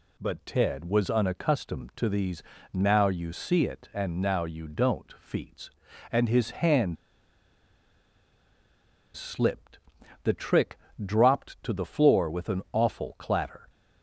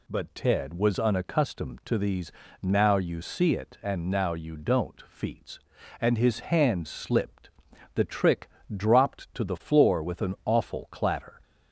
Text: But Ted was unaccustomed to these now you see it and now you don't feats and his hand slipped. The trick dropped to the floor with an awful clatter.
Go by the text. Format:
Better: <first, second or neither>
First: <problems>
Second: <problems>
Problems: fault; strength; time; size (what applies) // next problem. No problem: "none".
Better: second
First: pauses between "these" and "now"; slight; at 2.4 s; 0.32 s long // pauses between "hand" and "slipped"; strong; at 6.9 s; 2.2 s long // pauses between "trick" and "dropped"; slight; at 10.7 s; 0.26 s long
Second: pauses between "these" and "now"; slight; at 2.3 s; 0.32 s long // pauses between "trick" and "dropped"; slight; at 8.4 s; 0.26 s long